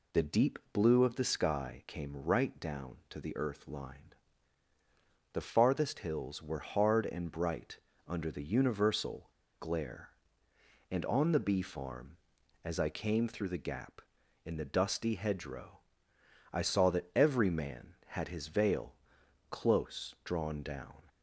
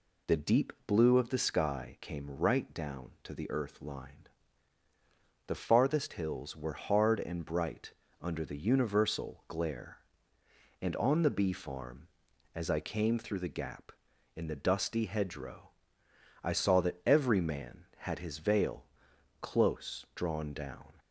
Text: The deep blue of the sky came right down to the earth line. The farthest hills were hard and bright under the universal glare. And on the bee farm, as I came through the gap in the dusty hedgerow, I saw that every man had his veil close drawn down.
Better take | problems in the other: second | pauses between "bright" and "under"; slight; at 7.7 s; 0.30 s long; slight in the second // pauses between "universal" and "glare"; slight; at 9.3 s; 0.29 s long // pauses between "veil" and "close"; noticeable; at 18.9 s; 0.54 s long; noticeable in the second

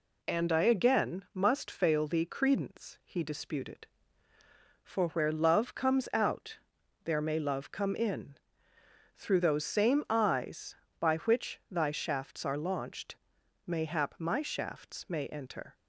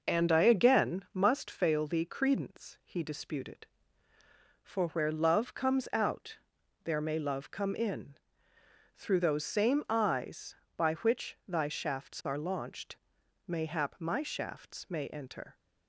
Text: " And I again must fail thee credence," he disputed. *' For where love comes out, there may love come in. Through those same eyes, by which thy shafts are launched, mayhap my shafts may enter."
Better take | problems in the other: first | starts louder than the rest; noticeable; until 1.4 s; 6 dB

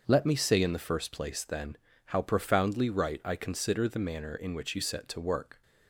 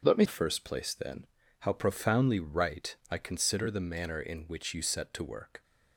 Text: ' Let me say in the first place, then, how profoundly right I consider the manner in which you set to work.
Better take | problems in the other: first | starts louder than the rest; until 1.0 s; 7 dB; also in the first // skips "say in the"; at 0.2 s // pauses between "right" and "I"; slight; at 2.9 s; 0.16 s long

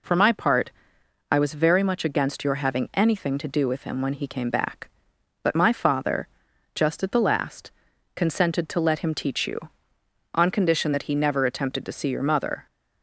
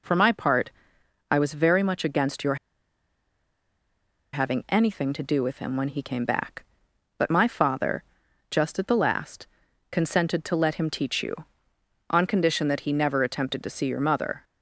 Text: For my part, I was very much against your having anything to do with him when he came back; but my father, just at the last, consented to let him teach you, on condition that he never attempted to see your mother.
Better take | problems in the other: first | pauses between "your" and "having"; strong; at 2.5 s; 1.7 s long

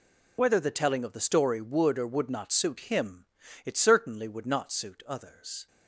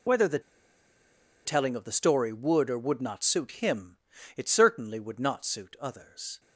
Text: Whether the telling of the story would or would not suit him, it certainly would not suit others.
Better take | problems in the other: first | pauses between "the" and "telling"; at 0.3 s; 1.0 s long

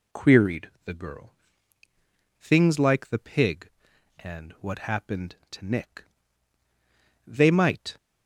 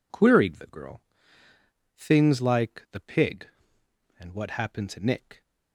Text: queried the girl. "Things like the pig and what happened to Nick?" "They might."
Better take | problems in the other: first | stops before "They might"; at 5.4 s

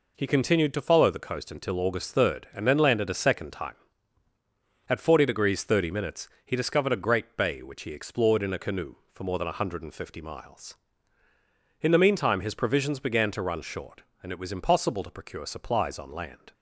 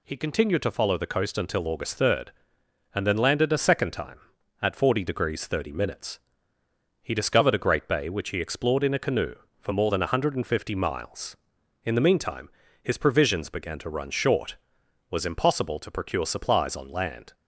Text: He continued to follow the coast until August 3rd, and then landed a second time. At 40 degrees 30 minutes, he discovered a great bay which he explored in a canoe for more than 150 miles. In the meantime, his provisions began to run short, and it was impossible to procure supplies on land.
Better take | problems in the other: first | skips "and it"; at 14.8 s

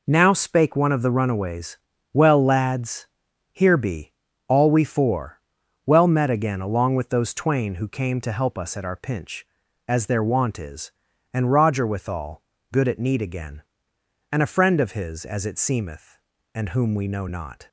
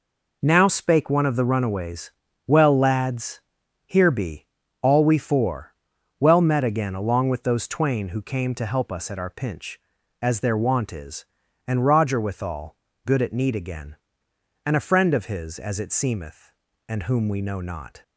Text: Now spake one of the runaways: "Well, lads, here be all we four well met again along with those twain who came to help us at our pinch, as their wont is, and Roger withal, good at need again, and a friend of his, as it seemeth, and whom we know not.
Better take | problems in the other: neither | pauses between "be" and "all"; the same in both // pauses between "four" and "well"; noticeable; the same in both

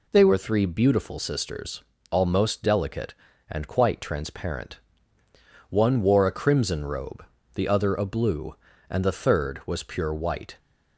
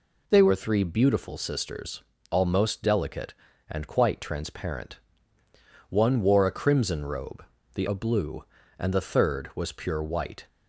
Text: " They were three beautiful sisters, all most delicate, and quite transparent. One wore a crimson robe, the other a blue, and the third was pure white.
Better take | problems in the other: first | skips "other"; at 7.8 s

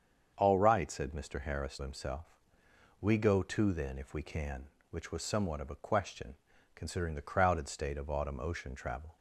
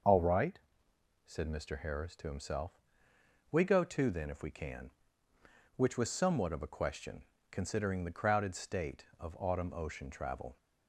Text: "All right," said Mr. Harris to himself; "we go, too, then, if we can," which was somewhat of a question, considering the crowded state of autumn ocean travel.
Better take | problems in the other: second | starts louder than the rest; strong; until 1.3 s; 7 dB // skips "to"; at 1.7 s

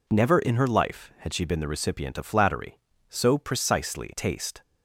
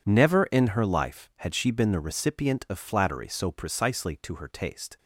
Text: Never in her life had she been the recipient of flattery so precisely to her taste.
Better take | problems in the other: second | skips "to her"; at 4.1 s

